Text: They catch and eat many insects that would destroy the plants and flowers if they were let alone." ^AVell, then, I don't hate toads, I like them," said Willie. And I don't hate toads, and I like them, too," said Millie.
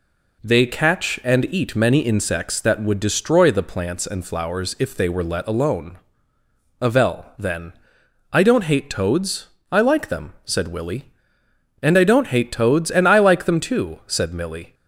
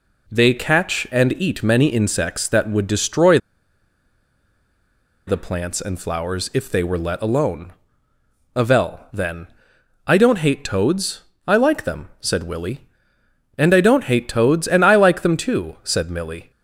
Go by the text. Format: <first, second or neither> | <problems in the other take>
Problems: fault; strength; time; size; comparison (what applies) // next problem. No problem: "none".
first | pauses between "destroy" and "the"; strong; at 3.3 s; 1.8 s long